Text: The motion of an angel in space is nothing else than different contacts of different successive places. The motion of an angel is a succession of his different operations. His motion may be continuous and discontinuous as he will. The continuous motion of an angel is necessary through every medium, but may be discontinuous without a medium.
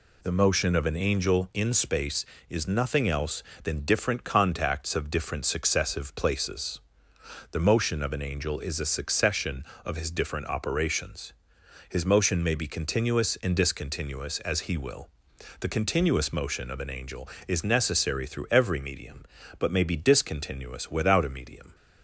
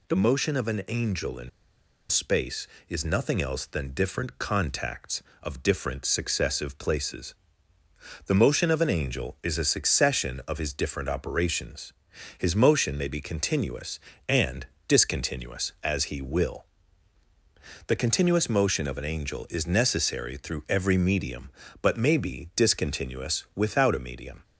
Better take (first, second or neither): first